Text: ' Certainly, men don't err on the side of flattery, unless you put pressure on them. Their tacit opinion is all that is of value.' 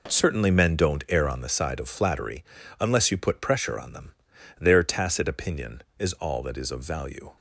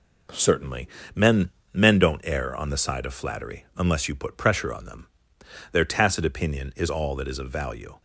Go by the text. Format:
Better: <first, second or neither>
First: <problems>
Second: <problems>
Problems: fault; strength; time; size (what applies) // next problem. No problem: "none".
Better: first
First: none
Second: says "men" twice; at 1.7 s